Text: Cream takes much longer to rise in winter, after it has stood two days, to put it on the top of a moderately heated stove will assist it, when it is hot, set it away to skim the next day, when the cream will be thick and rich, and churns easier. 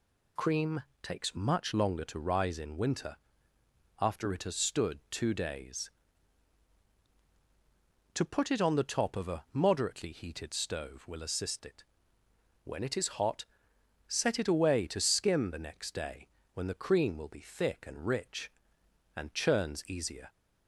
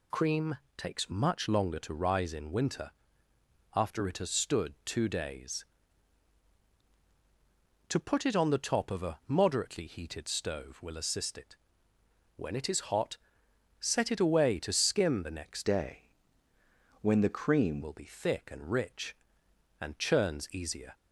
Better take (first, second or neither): first